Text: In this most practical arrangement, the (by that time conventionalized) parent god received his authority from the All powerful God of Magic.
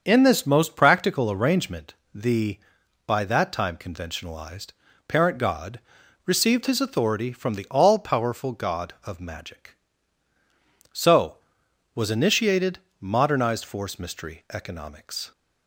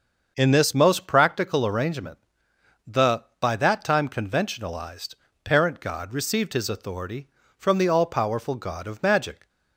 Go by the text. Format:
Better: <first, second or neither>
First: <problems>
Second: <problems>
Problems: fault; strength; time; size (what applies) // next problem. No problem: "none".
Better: second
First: starts louder than the rest; until 1.0 s; 6.5 dB // pauses between "god" and "received"; at 5.8 s; 0.44 s long // goes on to say "So was initiated modernized force mystery economics"; strong; from 10.9 s on; 4.3 s long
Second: starts louder than the rest; until 1.3 s; 6.5 dB